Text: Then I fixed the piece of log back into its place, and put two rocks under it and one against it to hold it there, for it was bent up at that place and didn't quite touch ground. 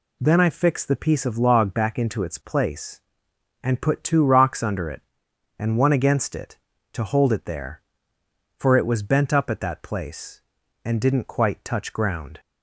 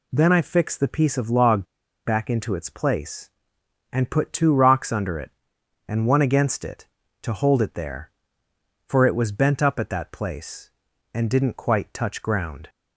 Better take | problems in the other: first | pauses between "log" and "back"; at 1.6 s; 0.39 s long

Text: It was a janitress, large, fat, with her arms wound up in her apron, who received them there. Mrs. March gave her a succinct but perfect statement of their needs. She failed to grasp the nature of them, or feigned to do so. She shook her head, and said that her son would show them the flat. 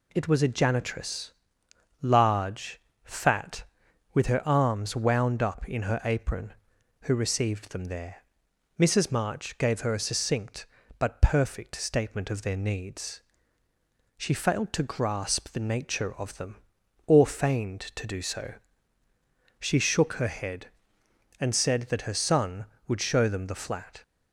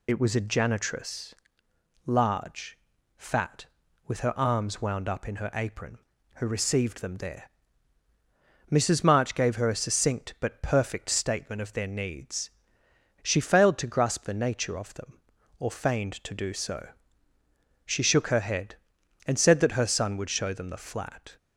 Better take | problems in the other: first | loses the start of "It"; at 0.0 s; 45 ms

